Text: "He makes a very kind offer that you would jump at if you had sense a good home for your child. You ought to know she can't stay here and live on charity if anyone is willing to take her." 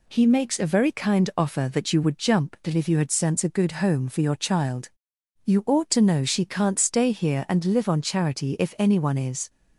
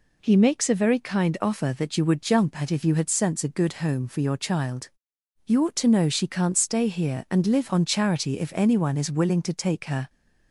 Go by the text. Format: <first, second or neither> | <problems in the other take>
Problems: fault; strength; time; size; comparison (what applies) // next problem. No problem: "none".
second | stops before "willing to take her"; at 9.4 s